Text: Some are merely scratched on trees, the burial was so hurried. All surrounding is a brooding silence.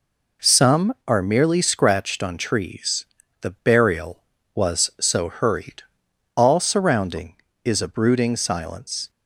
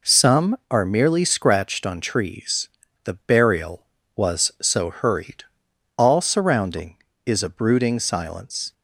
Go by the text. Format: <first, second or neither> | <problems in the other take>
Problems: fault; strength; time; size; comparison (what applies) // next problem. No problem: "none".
neither | none